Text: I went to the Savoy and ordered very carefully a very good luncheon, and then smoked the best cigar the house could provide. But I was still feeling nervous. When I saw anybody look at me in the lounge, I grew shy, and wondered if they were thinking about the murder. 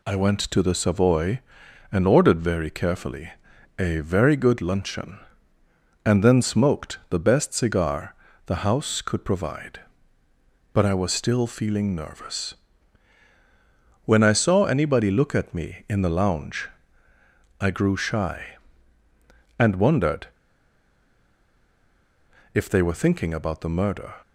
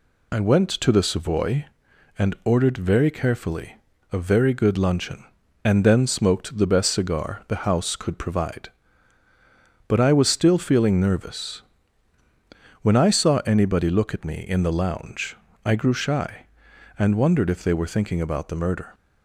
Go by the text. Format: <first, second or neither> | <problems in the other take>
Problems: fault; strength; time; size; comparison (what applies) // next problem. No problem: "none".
second | pauses between "carefully" and "a"; noticeable; at 3.3 s; 0.48 s long; slight in the second // pauses between "cigar" and "the"; slight; at 8.1 s; 0.32 s long // pauses between "wondered" and "if"; strong; at 20.2 s; 2.2 s long